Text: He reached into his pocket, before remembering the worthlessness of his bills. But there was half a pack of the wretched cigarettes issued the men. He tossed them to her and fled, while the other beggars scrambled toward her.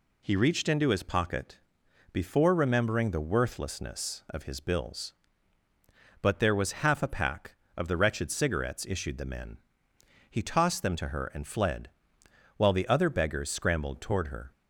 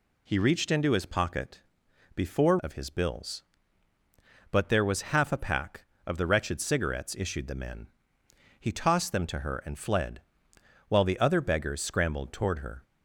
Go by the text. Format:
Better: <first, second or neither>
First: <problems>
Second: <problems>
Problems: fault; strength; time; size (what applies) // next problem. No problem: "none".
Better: first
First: none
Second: skips "remembering the worthlessness"; at 2.5 s